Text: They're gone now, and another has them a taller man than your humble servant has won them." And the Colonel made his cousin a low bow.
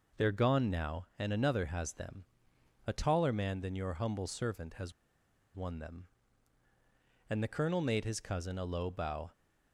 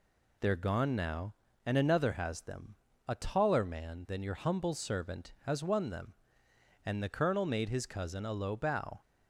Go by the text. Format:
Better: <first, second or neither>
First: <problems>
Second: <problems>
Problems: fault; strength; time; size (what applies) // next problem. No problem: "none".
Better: second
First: pauses between "them" and "a"; noticeable; at 2.2 s; 0.62 s long // pauses between "has" and "won"; noticeable; at 4.9 s; 0.63 s long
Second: pauses between "them" and "a"; slight; at 2.7 s; 0.34 s long